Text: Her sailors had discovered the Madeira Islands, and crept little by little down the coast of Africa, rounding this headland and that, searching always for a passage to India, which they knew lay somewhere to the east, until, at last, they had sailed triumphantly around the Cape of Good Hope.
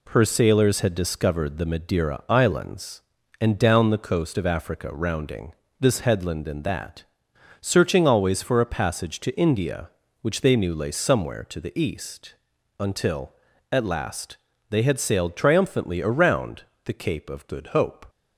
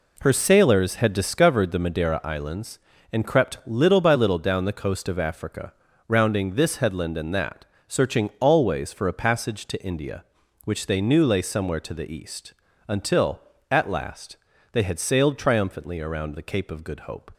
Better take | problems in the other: second | skips "crept little by little"; at 3.5 s // pauses between "rounding" and "this"; slight; at 5.5 s; 0.26 s long // pauses between "around" and "the"; slight; at 16.6 s; 0.20 s long

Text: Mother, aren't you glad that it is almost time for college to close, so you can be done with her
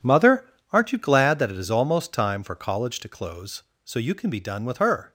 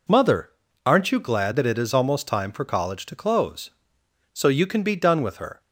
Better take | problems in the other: second | gets quieter; strong; throughout; 13.5 dB

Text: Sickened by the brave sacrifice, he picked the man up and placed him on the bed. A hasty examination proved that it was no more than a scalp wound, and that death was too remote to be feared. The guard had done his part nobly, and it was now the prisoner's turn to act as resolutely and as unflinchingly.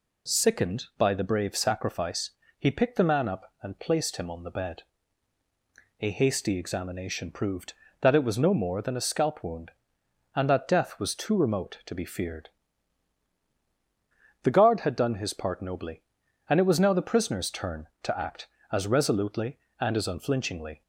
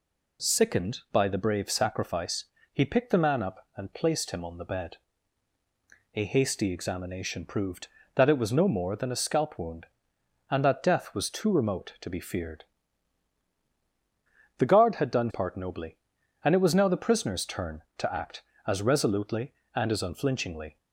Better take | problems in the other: first | skips "his"; at 15.2 s

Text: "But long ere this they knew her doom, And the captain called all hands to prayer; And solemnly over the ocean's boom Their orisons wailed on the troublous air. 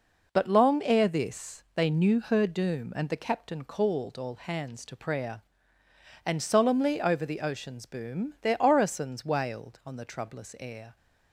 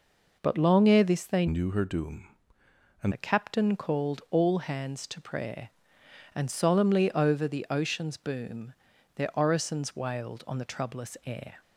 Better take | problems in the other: first | changes voice from "knew" to "And"; from 1.4 to 3.1 s; 1.7 s long // pauses between "boom" and "Their"; at 8.7 s; 0.42 s long

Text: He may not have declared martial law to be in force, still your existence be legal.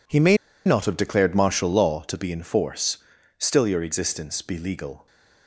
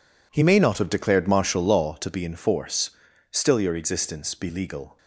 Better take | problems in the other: second | pauses between "may" and "not"; slight; at 0.3 s; 0.29 s long

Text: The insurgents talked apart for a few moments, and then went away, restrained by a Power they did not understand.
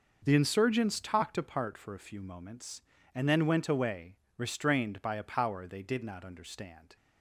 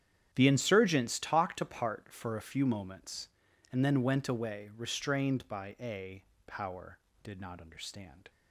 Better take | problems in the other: first | starts louder than the rest; strong; until 1.3 s; 9.5 dB // pauses between "a" and "Power"; slight; at 6.2 s; 0.22 s long // skips "they"; at 7.1 s

